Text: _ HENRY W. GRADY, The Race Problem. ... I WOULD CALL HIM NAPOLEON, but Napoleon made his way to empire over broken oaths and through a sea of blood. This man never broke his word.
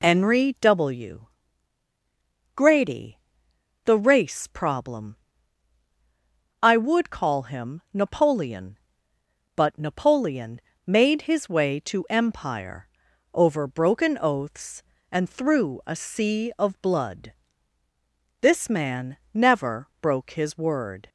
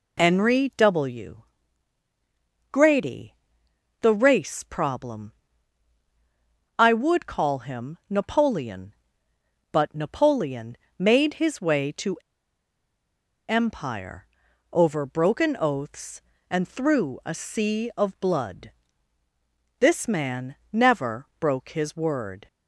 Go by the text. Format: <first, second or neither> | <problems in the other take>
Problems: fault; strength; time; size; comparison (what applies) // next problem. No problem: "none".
first | pauses between "Napoleon" and "made"; slight; at 10.7 s; 0.22 s long; slight in the first // pauses between "to" and "empire"; strong; at 12.1 s; 1.3 s long // pauses between "empire" and "over"; noticeable; at 14.2 s; 0.48 s long; noticeable in the first // pauses between "man" and "never"; slight; at 20.5 s; 0.18 s long; slight in the first